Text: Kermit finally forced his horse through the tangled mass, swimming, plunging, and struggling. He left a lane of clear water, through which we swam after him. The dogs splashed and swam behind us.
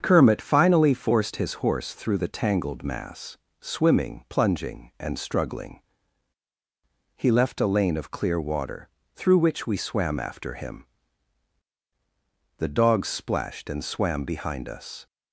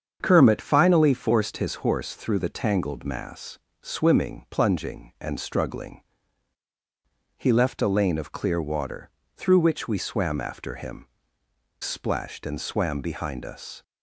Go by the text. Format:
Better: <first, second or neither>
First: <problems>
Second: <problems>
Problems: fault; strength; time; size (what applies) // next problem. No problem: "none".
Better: first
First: starts louder than the rest; strong; until 1.0 s; 7 dB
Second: starts louder than the rest; strong; until 1.2 s; 7.5 dB // skips "The dogs"; at 11.4 s